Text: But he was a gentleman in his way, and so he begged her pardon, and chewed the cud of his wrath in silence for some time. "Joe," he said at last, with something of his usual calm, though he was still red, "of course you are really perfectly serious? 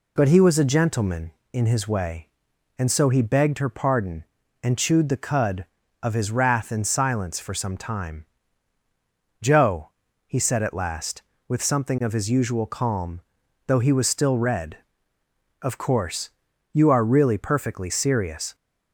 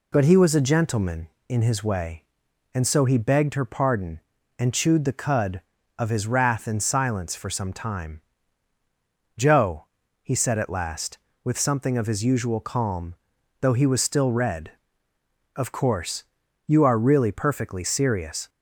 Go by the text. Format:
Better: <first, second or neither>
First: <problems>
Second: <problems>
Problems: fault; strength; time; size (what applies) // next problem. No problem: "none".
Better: neither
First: pauses between "course" and "you"; at 16.3 s; 0.42 s long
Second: pauses between "course" and "you"; at 16.2 s; 0.42 s long